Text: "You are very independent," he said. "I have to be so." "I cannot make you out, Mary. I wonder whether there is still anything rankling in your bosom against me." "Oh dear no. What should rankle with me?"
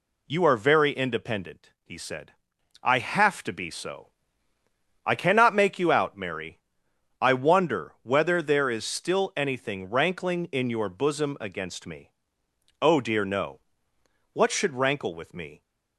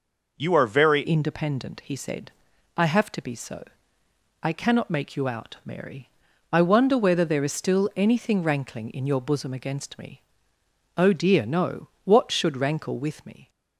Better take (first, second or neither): first